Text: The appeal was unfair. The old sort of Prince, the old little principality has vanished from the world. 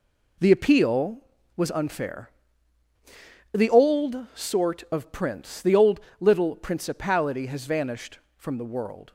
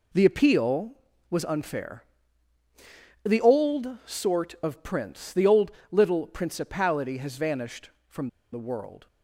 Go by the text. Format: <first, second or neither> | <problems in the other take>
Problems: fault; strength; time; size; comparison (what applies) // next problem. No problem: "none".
first | pauses between "old" and "little"; slight; at 5.7 s; 0.18 s long; slight in the first // pauses between "from" and "the"; slight; at 8.2 s; 0.24 s long